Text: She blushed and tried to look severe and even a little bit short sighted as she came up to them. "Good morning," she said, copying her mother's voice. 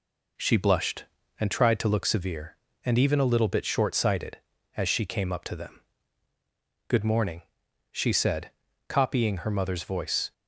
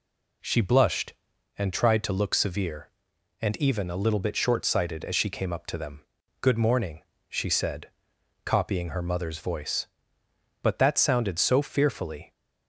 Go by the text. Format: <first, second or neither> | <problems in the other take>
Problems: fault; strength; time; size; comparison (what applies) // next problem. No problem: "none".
first | goes on to say "But that sounded so fearfully"; strong; from 10.6 s on; 1.7 s long